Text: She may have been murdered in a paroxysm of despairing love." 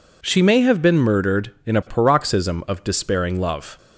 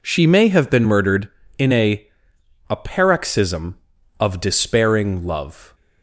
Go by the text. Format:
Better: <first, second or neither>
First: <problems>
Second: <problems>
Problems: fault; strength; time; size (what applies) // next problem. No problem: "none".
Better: first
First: none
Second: says "a" twice; at 2.6 s